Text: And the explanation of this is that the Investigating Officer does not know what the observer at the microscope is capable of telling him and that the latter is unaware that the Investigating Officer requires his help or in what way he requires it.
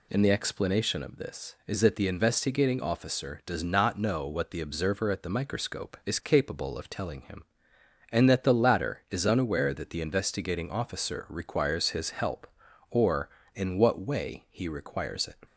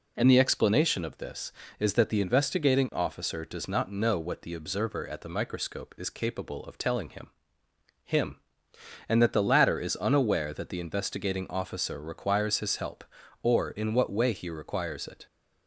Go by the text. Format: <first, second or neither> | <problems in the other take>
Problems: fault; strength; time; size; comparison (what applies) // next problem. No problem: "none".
first | says "him" twice; at 8.0 s